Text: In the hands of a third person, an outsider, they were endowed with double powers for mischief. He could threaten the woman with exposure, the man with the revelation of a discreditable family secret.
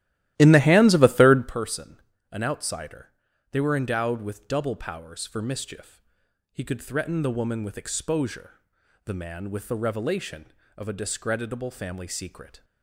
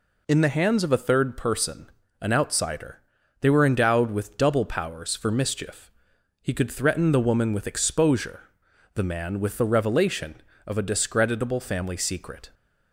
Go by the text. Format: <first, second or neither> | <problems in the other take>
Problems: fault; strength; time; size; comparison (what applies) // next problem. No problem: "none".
second | starts louder than the rest; strong; until 1.6 s; 14.5 dB